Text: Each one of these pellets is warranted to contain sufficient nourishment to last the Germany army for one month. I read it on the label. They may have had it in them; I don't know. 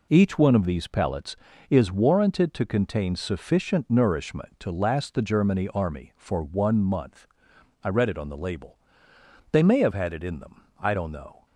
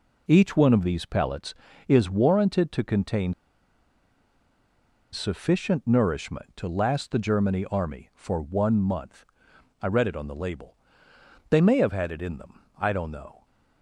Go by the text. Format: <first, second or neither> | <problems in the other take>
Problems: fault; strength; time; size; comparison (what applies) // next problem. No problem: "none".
first | pauses between "contain" and "sufficient"; strong; at 3.3 s; 1.8 s long